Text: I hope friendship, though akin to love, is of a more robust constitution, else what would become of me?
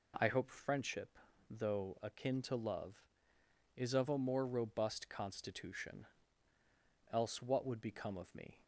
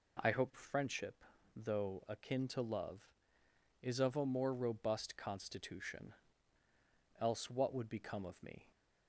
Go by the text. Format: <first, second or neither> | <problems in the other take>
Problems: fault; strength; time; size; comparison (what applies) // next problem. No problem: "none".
neither | none